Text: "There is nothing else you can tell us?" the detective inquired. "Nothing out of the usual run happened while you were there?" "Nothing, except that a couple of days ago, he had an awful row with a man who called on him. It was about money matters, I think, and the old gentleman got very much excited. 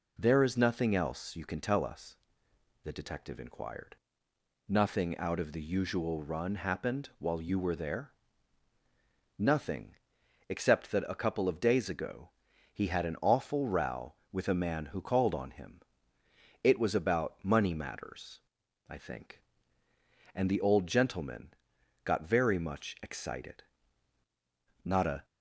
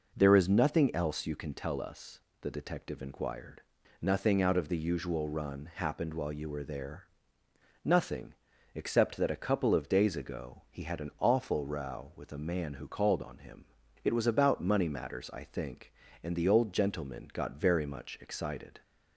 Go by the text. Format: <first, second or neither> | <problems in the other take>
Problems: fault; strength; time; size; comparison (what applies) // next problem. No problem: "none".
second | pauses between "gentleman" and "got"; noticeable; at 21.5 s; 0.52 s long // goes on to say "Not a"; slight; from 24.8 s on; 0.42 s long